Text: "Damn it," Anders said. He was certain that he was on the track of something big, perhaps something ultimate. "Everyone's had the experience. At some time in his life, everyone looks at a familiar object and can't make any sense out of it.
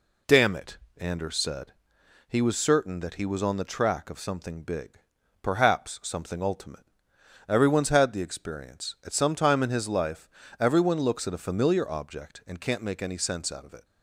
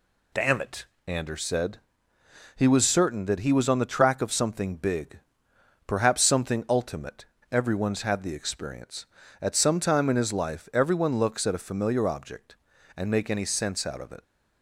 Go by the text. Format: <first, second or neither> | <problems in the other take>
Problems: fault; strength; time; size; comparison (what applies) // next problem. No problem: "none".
first | skips "can't"; at 13.1 s